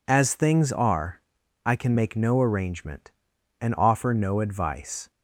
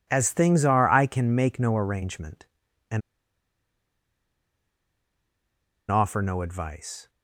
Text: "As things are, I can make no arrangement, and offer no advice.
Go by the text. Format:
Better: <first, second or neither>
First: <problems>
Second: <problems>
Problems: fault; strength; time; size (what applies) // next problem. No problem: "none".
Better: first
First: none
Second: pauses between "and" and "offer"; strong; at 3.0 s; 2.9 s long